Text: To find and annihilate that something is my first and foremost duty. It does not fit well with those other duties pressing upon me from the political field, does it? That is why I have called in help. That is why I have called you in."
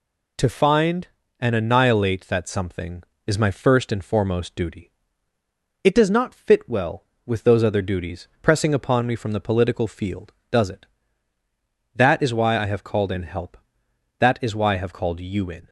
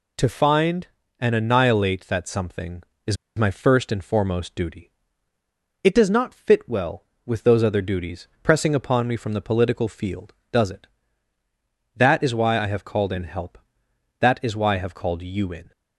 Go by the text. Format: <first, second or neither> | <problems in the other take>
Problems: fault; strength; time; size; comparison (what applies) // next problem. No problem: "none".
first | pauses between "is" and "my"; slight; at 3.1 s; 0.21 s long